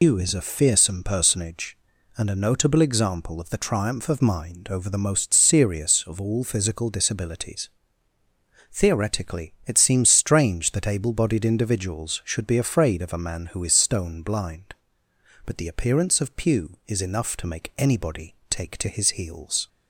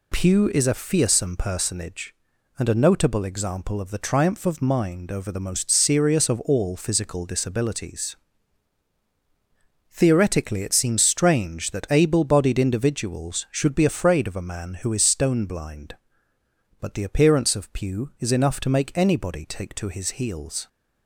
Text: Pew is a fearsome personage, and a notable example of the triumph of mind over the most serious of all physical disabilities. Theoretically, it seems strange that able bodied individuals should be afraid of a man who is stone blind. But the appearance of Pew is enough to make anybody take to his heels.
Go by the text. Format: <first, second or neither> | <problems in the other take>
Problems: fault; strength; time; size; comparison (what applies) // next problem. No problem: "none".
second | loses the start of "Pew"; at 0.0 s; 160 ms